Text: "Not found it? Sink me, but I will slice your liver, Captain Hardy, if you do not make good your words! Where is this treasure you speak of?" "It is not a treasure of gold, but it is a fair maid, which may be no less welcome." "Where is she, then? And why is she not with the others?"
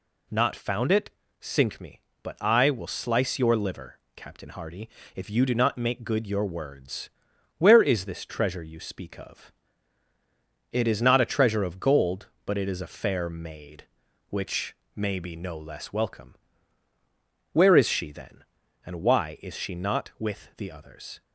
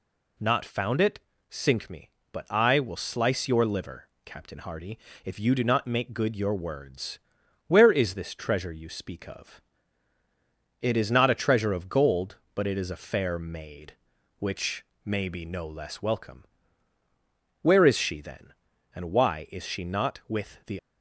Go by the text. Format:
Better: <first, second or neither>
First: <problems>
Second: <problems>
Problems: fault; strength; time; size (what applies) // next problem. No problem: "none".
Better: first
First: pauses between "which" and "may"; slight; at 14.7 s; 0.20 s long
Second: pauses between "which" and "may"; slight; at 14.8 s; 0.20 s long // stops before "others"; at 20.7 s